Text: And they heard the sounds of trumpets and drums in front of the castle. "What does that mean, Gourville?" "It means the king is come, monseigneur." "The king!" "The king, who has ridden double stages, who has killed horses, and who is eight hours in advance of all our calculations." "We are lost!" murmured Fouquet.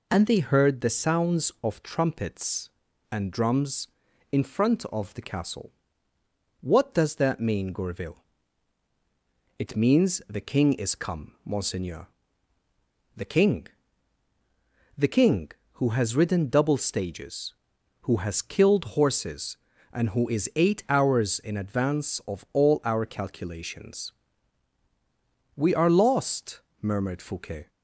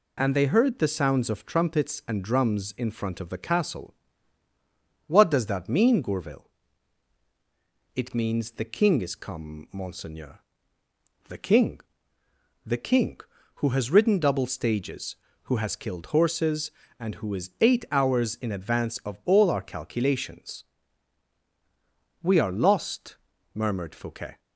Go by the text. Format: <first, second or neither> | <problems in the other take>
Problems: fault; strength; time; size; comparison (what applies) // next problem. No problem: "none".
neither | none